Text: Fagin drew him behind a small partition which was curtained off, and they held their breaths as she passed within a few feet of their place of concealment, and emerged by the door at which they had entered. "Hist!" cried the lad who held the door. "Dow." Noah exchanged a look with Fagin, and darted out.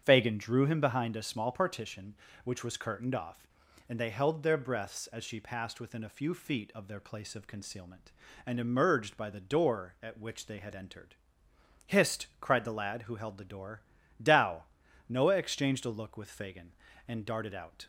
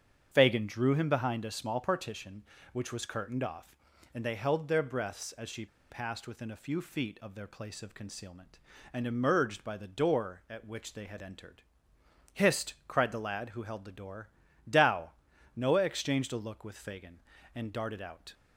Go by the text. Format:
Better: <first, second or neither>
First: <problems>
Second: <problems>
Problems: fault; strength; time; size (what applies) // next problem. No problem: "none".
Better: first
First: starts louder than the rest; strong; until 1.0 s; 7.5 dB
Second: starts louder than the rest; strong; until 1.3 s; 7.5 dB // pauses between "she" and "passed"; slight; at 5.6 s; 0.24 s long